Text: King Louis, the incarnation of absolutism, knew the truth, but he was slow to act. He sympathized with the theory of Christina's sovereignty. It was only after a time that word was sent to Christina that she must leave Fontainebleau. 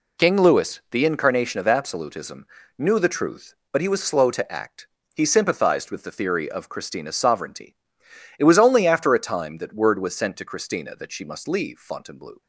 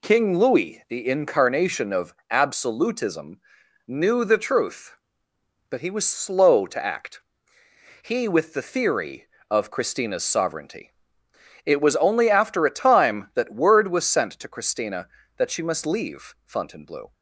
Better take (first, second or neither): first